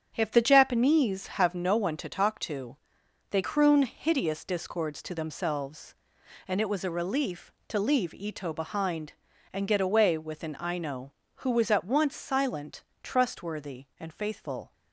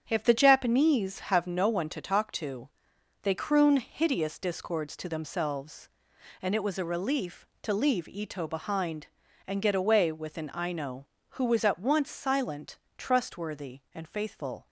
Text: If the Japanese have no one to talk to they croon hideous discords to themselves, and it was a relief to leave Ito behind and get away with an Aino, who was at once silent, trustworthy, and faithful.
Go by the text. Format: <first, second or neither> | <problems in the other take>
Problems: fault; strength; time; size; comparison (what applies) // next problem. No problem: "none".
neither | starts louder than the rest; strong; the same in both // pauses between "to" and "they"; noticeable; the same in both